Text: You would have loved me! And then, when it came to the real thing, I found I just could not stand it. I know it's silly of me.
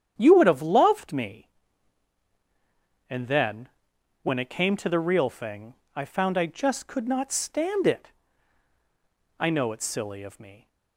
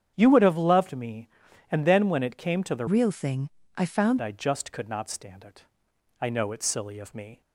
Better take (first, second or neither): first